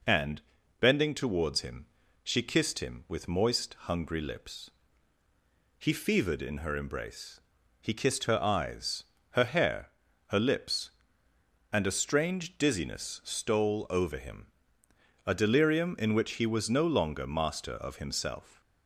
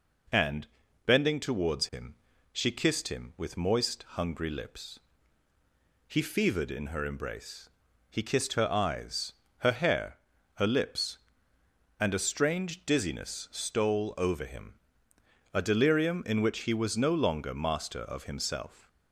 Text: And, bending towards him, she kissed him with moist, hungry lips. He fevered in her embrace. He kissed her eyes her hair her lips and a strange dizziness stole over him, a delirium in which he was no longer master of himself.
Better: neither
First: pauses between "eyes" and "her"; slight; at 9.0 s; 0.29 s long // pauses between "hair" and "her"; at 9.8 s; 0.40 s long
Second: pauses between "eyes" and "her"; slight; at 9.3 s; 0.28 s long // pauses between "hair" and "her"; at 10.1 s; 0.40 s long

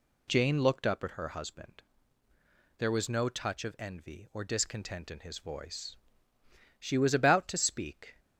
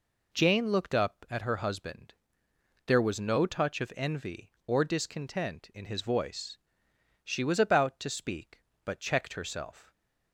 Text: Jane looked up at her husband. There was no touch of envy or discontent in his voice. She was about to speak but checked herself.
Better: second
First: stops before "but checked herself"; at 8.1 s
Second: none

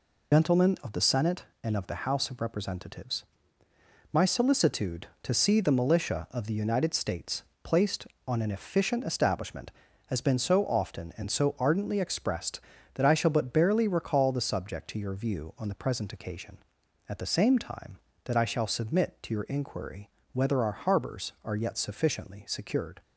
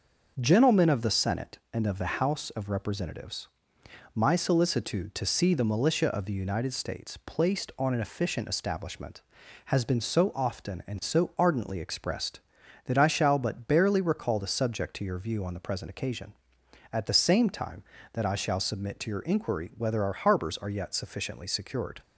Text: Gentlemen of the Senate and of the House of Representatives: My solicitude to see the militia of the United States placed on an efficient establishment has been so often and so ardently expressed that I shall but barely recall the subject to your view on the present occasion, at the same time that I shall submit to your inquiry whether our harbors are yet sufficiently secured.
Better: second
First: loses the start of "Gentlemen"; at 0.3 s; 60 ms // pauses between "States" and "placed"; slight; at 7.4 s; 0.22 s long // pauses between "inquiry" and "whether"; slight; at 20.0 s; 0.26 s long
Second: none

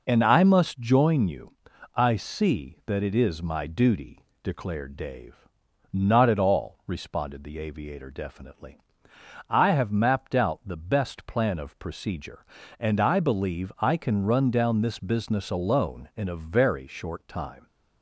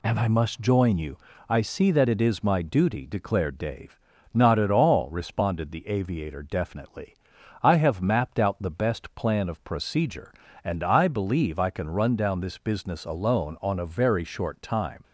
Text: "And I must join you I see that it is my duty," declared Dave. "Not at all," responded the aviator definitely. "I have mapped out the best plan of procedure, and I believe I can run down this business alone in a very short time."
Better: first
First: pauses between "you" and "I"; at 1.5 s; 0.40 s long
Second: pauses between "you" and "I"; slight; at 1.1 s; 0.32 s long // says "on" for "in"; at 13.6 s

